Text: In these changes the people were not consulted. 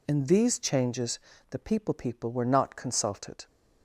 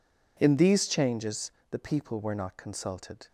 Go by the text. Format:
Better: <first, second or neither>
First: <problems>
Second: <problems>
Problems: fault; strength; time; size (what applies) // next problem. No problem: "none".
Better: second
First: pauses between "changes" and "the"; slight; at 1.1 s; 0.32 s long // says "people" twice; at 1.9 s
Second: pauses between "changes" and "the"; slight; at 1.4 s; 0.22 s long